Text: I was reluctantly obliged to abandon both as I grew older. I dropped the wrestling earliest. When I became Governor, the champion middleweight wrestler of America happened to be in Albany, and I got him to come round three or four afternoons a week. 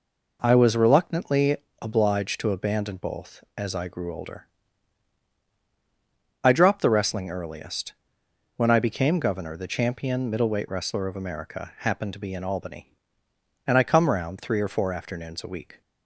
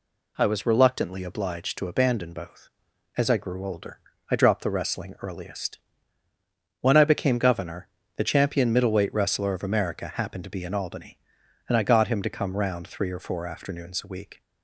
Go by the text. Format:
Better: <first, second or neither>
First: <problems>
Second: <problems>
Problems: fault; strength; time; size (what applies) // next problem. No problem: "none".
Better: second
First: pauses between "reluctantly" and "obliged"; slight; at 1.5 s; 0.26 s long // skips "got him to"; at 13.8 s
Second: none